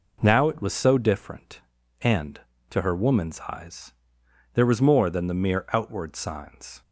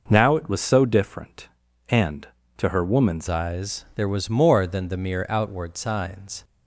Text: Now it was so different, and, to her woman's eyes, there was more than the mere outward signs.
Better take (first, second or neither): first